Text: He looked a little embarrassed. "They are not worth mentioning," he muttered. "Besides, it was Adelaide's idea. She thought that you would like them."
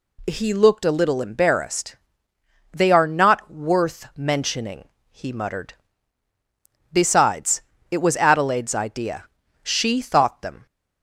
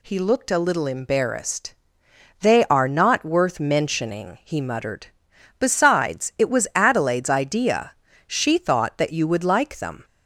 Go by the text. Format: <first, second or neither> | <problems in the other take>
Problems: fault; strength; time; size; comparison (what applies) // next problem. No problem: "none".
second | skips "that you would like"; at 10.4 s